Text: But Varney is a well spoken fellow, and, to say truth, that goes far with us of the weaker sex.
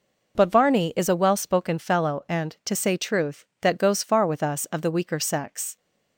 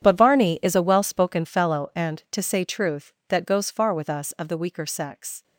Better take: first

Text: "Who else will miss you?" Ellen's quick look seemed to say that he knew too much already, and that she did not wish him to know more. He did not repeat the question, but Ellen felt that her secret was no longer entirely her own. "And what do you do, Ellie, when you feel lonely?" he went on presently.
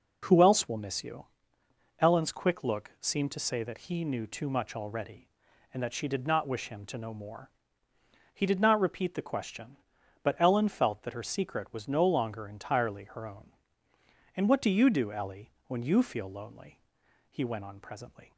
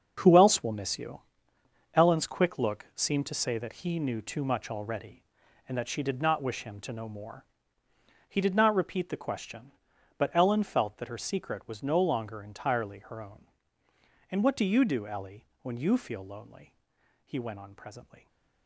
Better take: first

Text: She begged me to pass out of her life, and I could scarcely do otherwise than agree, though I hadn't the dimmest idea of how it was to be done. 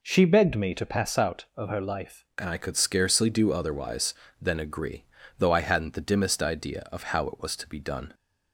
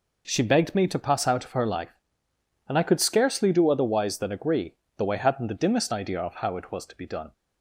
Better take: second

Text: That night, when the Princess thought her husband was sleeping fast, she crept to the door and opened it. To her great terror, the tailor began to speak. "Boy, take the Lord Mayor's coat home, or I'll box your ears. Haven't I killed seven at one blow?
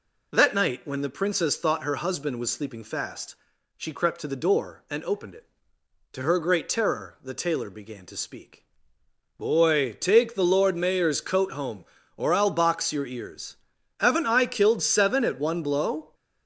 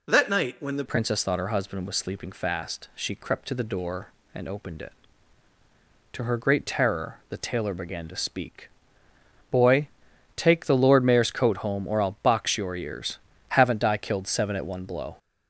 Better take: first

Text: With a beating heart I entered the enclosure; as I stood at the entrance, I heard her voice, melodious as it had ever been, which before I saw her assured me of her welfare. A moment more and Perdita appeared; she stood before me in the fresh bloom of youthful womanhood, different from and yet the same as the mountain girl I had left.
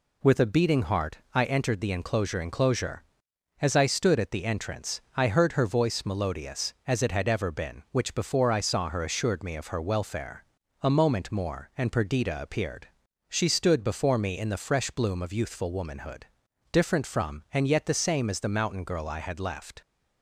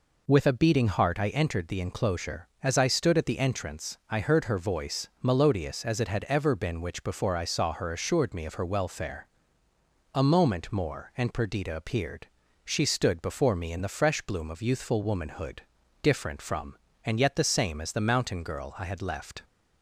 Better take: second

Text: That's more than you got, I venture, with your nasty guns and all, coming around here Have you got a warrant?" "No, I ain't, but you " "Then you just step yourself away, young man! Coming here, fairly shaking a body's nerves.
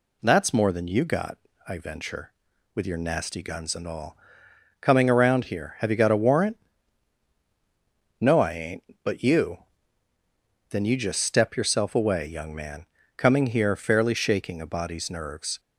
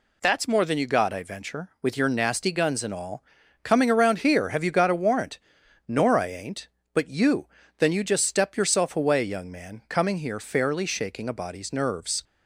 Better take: first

